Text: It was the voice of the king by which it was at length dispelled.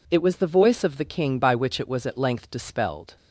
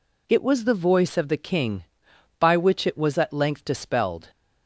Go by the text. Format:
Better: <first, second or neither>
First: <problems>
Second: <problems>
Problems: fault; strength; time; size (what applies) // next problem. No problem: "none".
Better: neither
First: none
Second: none